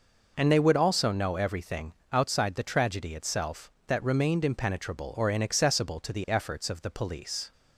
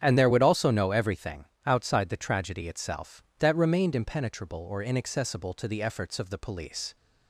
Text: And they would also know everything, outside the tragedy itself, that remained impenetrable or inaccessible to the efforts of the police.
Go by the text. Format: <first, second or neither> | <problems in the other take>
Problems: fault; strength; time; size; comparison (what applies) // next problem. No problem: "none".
first | starts louder than the rest; strong; until 1.0 s; 8.5 dB // says "there" for "they"; at 0.1 s